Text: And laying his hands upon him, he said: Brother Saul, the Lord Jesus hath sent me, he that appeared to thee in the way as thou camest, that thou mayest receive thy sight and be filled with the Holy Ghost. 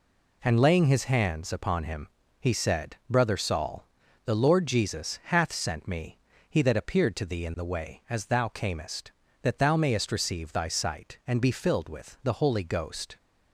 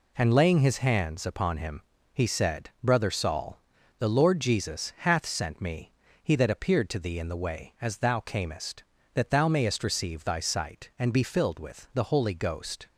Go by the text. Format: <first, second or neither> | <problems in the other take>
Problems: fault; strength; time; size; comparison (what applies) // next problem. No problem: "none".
neither | none